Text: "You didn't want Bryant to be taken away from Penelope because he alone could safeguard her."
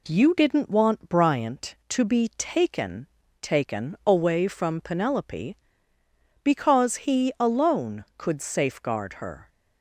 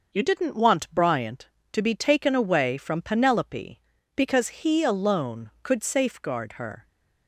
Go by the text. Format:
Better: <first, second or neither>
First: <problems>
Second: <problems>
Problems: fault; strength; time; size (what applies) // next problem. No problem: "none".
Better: second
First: says "taken" twice; at 3.4 s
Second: none